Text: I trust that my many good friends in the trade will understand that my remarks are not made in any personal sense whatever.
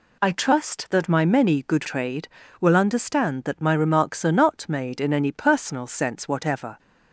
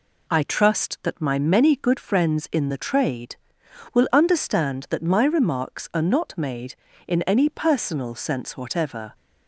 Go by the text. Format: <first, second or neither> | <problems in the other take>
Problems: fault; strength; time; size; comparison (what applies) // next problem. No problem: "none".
second | skips "friends in the"; at 1.8 s